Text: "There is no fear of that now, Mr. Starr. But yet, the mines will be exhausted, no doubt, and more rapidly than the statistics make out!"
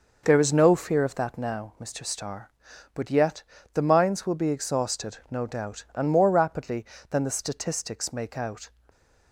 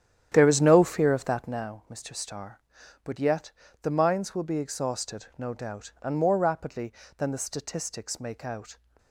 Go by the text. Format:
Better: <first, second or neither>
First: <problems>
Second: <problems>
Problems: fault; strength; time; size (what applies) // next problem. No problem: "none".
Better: first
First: none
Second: starts louder than the rest; strong; until 1.7 s; 10 dB